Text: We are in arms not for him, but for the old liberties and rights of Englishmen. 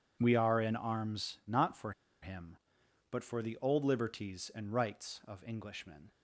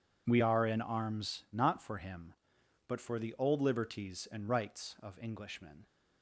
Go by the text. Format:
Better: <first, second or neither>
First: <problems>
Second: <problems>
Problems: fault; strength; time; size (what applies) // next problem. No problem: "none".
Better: second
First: pauses between "for" and "him"; slight; at 1.9 s; 0.30 s long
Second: none